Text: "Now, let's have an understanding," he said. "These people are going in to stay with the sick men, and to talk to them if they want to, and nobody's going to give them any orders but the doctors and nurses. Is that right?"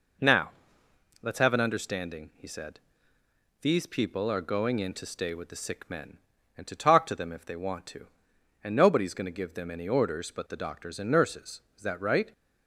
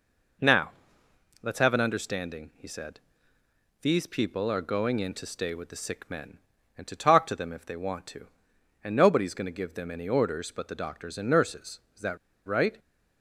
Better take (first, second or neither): first